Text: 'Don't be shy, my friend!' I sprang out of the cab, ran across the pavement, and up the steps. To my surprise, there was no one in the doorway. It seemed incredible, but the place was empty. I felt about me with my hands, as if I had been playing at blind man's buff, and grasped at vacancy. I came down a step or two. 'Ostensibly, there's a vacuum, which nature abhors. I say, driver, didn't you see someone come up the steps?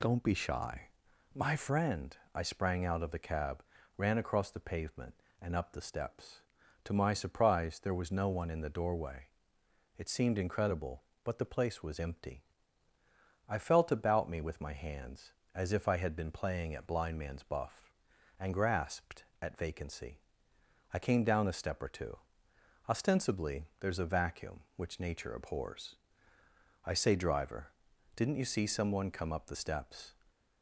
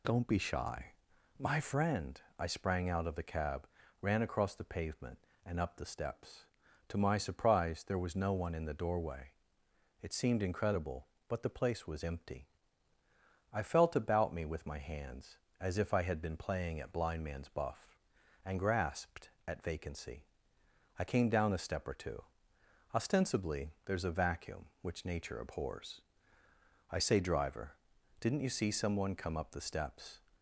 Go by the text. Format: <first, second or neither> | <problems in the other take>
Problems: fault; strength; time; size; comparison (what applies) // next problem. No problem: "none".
neither | none